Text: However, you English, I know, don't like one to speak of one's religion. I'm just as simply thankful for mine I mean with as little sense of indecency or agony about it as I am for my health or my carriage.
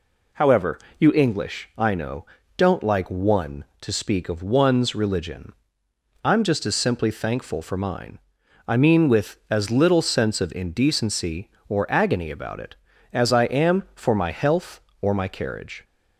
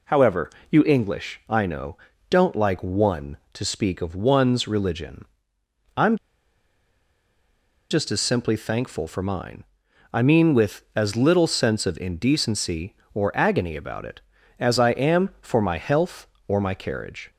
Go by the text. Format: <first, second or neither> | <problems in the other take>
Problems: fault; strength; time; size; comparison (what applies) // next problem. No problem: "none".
first | pauses between "I'm" and "just"; strong; at 6.1 s; 1.7 s long // pauses between "mine" and "I"; noticeable; at 9.6 s; 0.48 s long; noticeable in the first